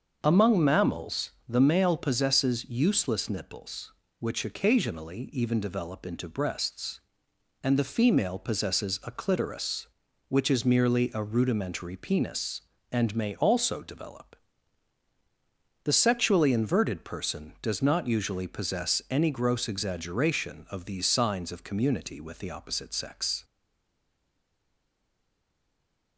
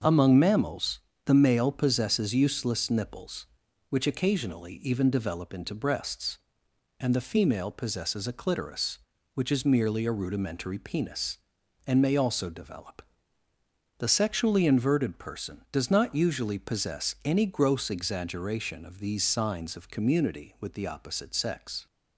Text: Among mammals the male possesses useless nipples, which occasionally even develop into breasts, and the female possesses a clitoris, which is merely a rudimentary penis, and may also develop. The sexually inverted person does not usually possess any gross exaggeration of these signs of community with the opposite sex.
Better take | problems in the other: second | starts louder than the rest; until 1.2 s; 6.5 dB; also in the second // pauses between "mammals" and "the"; slight; at 1.3 s; 0.18 s long; slight in the second // stays silent after the last word; strong; from 23.4 s on; 2.7 s long

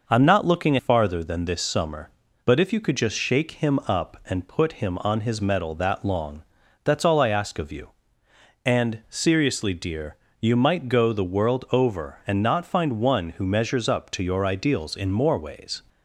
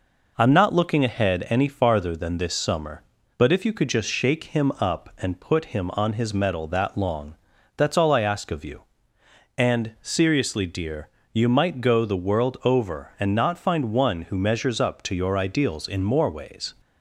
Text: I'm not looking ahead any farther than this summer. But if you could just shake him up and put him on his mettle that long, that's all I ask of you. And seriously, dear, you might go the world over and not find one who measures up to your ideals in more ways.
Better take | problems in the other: second | skips "ahead any"; at 0.7 s

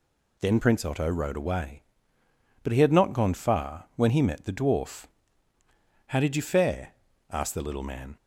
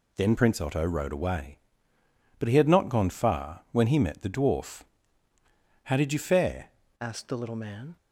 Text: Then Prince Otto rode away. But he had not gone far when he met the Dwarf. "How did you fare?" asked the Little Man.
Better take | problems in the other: first | changes voice at "asked"; from 7.0 s on; 0.9 s long

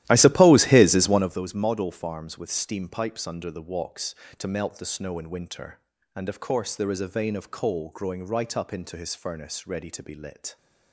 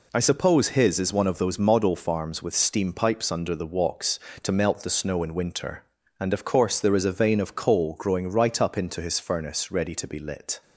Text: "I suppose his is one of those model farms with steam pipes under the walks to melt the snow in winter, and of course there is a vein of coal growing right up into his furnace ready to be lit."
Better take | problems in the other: second | starts louder than the rest; strong; until 1.4 s; 14 dB

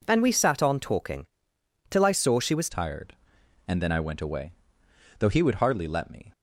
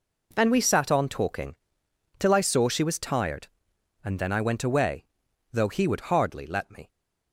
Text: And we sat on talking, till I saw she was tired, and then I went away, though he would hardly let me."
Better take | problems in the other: second | changes voice at "tired"; from 2.6 s on; 3.7 s long

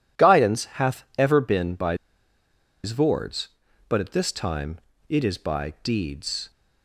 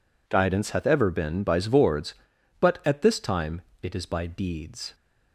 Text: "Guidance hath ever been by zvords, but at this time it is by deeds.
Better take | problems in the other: second | pauses between "by" and "zvords"; noticeable; at 1.9 s; 0.88 s long // pauses between "time" and "it"; slight; at 4.8 s; 0.28 s long; slight in the second

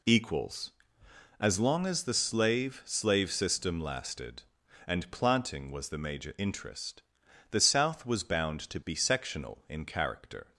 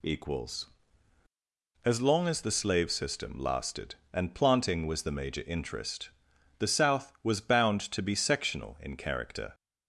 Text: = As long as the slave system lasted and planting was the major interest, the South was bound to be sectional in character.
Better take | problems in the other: second | says "slave" twice; at 2.8 s

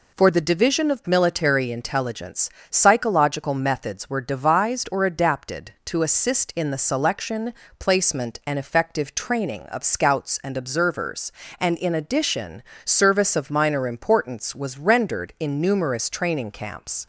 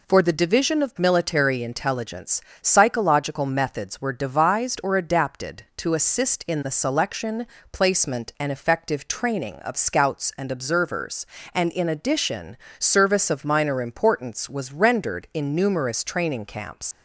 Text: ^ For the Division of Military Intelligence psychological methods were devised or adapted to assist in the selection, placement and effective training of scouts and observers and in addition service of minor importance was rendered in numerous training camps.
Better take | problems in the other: first | pauses between "Intelligence" and "psychological"; slight; at 2.4 s; 0.20 s long; slight in the first // pauses between "addition" and "service"; slight; at 12.5 s; 0.22 s long; slight in the first // leaves "camps" unfinished; at 16.9 s; 90 ms

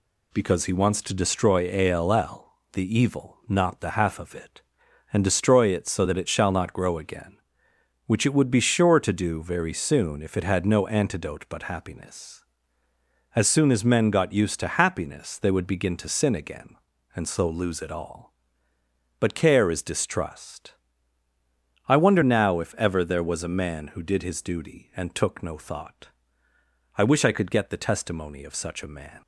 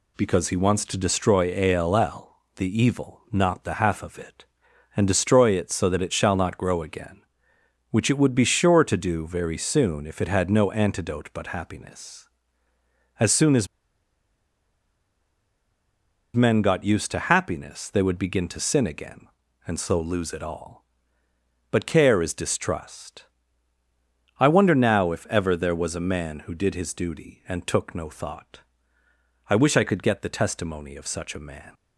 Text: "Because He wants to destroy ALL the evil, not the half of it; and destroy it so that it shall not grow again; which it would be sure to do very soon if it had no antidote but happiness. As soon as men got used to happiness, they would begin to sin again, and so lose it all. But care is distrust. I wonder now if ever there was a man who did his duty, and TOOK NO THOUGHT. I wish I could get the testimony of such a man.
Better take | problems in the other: first | pauses between "as" and "men"; strong; at 13.6 s; 2.6 s long

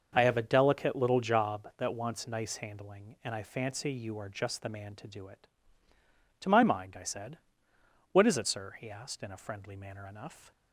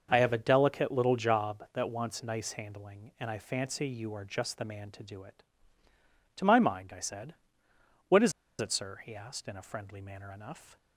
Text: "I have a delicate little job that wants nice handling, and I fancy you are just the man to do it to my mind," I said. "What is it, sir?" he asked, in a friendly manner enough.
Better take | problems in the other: first | starts louder than the rest; noticeable; until 1.1 s; 6 dB; also in the first // pauses between "is" and "it"; slight; at 8.3 s; 0.28 s long

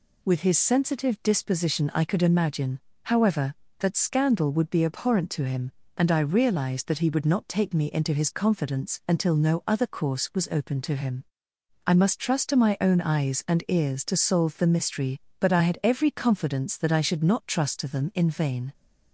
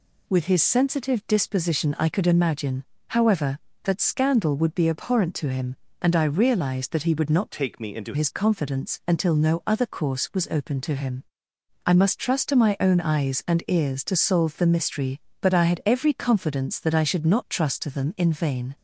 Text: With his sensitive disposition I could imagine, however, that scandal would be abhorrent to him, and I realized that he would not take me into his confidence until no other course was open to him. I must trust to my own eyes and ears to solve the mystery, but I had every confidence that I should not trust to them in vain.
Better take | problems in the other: first | changes voice from "take" to "into"; from 7.5 to 8.1 s; 0.6 s long

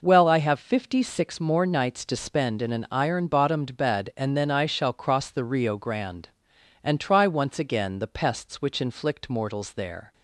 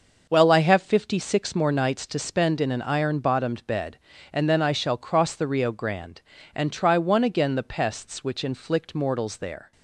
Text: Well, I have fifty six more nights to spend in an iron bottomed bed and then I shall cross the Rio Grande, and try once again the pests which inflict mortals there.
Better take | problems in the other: first | starts louder than the rest; noticeable; until 1.3 s; 6 dB // says "one" for "once"; at 6.9 s

